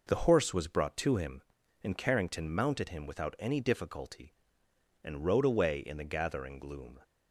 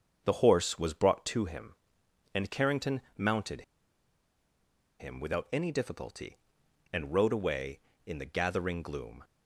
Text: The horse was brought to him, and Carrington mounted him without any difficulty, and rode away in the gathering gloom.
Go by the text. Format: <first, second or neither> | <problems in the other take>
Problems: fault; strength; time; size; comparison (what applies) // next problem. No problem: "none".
first | starts louder than the rest; until 1.2 s; 7 dB // pauses between "Carrington" and "mounted"; slight; at 3.0 s; 0.16 s long // pauses between "mounted" and "him"; strong; at 3.6 s; 1.3 s long